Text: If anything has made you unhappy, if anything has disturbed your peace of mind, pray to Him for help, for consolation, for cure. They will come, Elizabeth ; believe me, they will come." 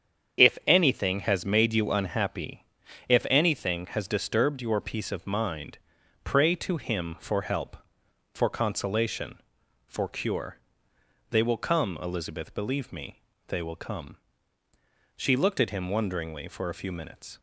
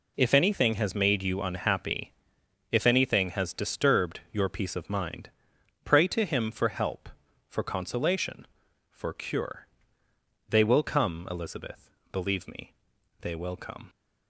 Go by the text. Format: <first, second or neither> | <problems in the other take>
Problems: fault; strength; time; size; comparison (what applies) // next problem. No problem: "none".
second | starts louder than the rest; strong; until 1.5 s; 8 dB // goes on to say "She looked at him wonderingly for a few minutes"; strong; from 15.1 s on; 2.2 s long